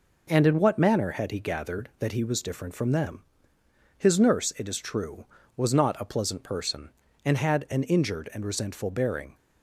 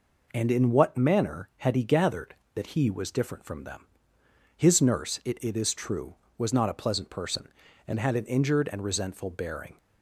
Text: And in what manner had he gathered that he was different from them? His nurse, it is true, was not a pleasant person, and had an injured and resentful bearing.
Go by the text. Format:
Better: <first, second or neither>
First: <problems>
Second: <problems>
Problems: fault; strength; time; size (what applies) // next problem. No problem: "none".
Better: first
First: none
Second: says "it" twice; at 5.4 s